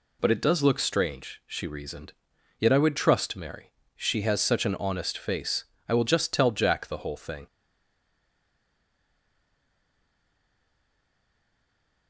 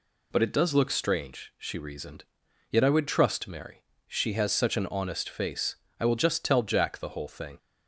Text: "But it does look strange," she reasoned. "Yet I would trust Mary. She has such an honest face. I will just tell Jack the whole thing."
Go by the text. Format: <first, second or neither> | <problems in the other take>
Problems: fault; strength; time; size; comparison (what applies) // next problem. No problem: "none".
second | stays silent after the last word; strong; from 7.4 s on; 4.6 s long